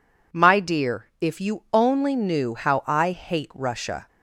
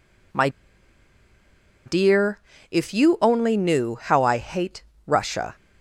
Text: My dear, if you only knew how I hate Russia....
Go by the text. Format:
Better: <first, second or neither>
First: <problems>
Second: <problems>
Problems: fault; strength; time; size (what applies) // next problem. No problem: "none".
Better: first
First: none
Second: pauses between "My" and "dear"; strong; at 0.4 s; 1.3 s long // pauses between "hate" and "Russia"; slight; at 4.8 s; 0.24 s long